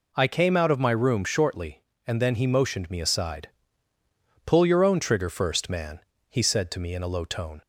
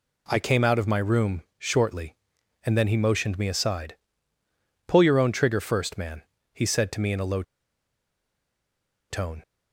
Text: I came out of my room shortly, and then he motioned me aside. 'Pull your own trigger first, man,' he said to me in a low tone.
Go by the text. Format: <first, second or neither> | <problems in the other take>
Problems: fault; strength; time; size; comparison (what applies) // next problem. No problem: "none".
first | pauses between "low" and "tone"; strong; at 7.4 s; 1.6 s long